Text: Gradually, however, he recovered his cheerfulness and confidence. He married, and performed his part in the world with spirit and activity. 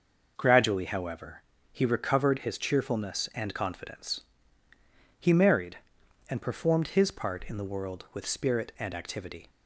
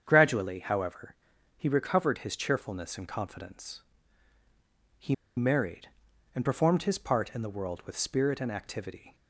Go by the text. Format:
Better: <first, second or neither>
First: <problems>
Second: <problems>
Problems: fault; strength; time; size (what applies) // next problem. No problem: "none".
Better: first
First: none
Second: starts louder than the rest; strong; until 1.0 s; 8 dB // pauses between "He" and "married"; slight; at 5.1 s; 0.22 s long